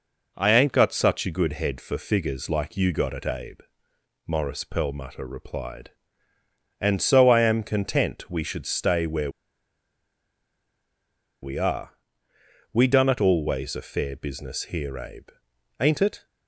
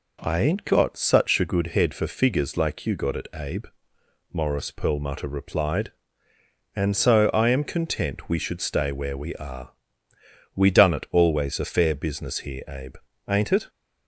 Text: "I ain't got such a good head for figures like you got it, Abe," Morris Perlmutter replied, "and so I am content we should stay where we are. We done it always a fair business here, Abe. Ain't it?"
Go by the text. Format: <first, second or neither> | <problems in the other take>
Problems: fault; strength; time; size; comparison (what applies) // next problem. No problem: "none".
second | pauses between "where" and "we"; strong; at 9.2 s; 2.1 s long